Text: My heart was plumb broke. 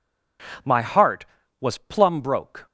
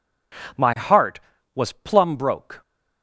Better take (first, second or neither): neither